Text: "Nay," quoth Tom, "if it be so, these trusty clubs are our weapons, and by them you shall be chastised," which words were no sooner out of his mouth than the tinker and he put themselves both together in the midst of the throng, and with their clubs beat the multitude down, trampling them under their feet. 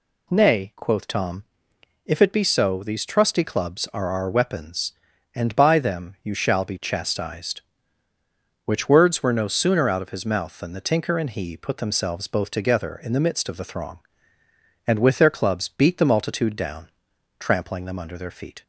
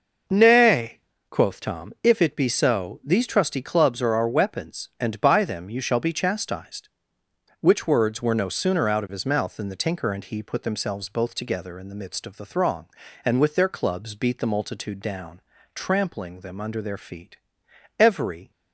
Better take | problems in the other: first | goes on to say "Every"; from 17.9 s on; 0.52 s long

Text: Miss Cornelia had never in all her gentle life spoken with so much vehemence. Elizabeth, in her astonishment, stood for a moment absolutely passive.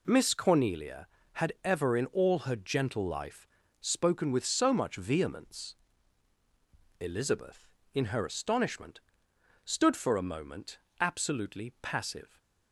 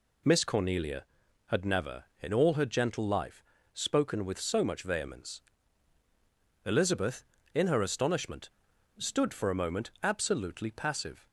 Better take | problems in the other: second | says "ever" for "never"; at 1.6 s // pauses between "life" and "spoken"; slight; at 3.4 s; 0.32 s long; slight in the second // pauses between "moment" and "absolutely"; slight; at 10.7 s; 0.22 s long

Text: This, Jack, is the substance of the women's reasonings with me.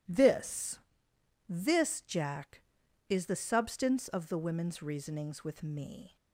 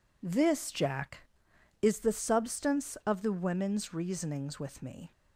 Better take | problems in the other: second | says "This" twice; at 1.4 s

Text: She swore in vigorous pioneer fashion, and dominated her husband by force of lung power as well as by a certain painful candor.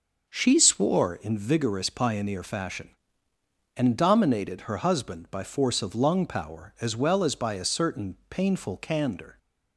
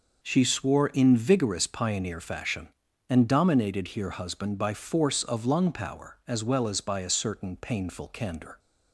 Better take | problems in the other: first | says "here" for "her"; at 3.8 s

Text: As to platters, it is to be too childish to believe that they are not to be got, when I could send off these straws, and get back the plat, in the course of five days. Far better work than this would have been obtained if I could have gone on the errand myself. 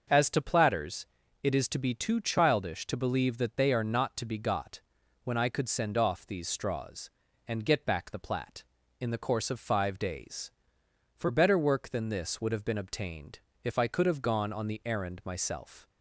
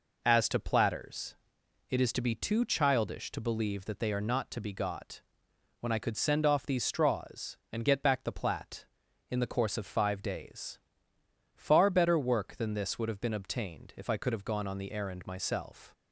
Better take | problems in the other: second | starts louder than the rest; until 1.4 s; 6.5 dB // says "For" for "Far"; at 11.1 s // pauses between "obtained" and "if"; slight; at 13.4 s; 0.22 s long

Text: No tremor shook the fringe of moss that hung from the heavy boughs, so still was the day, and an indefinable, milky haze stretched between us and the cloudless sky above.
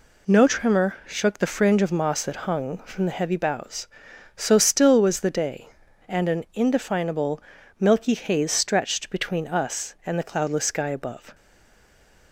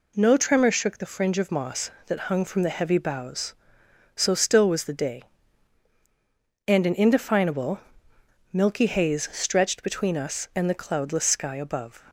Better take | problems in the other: second | stays silent after the last word; from 11.3 s on; 1.0 s long

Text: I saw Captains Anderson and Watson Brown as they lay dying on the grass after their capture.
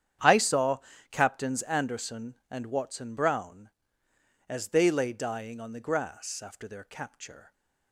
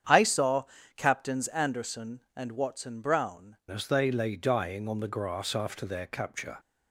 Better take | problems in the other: first | starts louder than the rest; strong; until 1.4 s; 8.5 dB; strong in the first // pauses between "saw" and "Captains"; slight; at 0.6 s; 0.32 s long; slight in the first // changes voice at "as"; from 3.7 s on; 2.8 s long

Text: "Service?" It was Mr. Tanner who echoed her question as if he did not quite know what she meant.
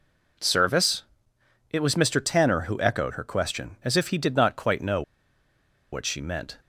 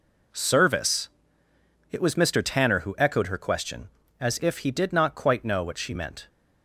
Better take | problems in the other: second | pauses between "know" and "what"; noticeable; at 5.0 s; 0.91 s long

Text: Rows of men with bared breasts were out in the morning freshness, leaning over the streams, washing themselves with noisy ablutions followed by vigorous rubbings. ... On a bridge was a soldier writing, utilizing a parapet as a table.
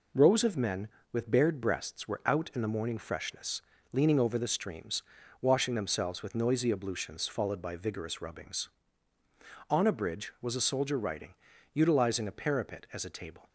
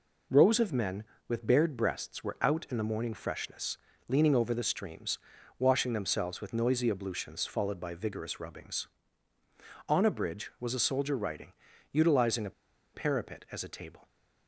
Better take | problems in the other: first | pauses between "a" and "parapet"; at 12.5 s; 0.43 s long

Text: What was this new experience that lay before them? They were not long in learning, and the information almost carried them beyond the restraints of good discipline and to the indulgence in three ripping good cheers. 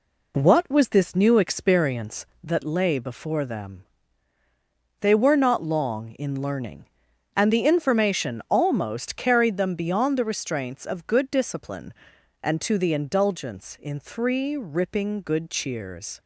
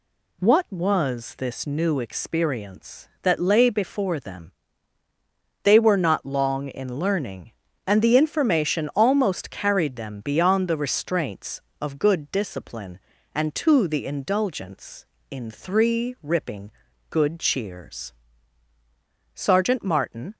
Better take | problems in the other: first | pauses between "ripping" and "good"; at 16.7 s; 0.40 s long // goes on to say "Sergeant Martin"; noticeable; from 19.3 s on; 1.0 s long

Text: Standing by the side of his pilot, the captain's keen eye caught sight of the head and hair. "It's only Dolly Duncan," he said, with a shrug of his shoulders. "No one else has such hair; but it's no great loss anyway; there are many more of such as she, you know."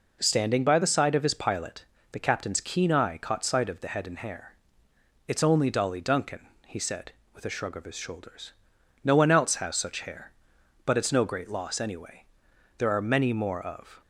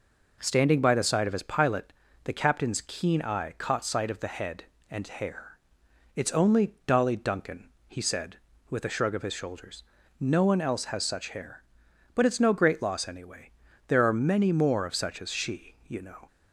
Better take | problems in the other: second | stops before "such as she you know"; at 14.0 s

